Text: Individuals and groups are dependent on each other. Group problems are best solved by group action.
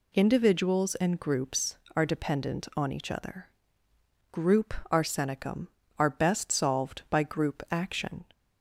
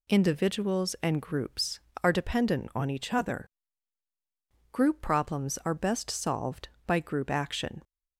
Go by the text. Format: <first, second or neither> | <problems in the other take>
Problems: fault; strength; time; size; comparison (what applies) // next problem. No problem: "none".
second | says "arsenicum" for "problems"; at 4.9 s